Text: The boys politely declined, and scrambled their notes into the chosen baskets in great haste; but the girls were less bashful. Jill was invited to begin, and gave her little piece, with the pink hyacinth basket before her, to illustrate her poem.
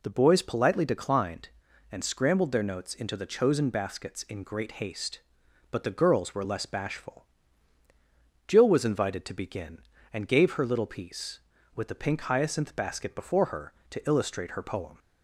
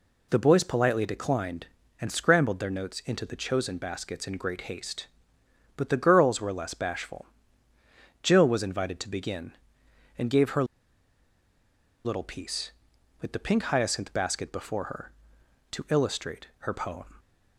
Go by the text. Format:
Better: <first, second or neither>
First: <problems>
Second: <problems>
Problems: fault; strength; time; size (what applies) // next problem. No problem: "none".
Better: first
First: none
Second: pauses between "her" and "little"; strong; at 10.6 s; 1.4 s long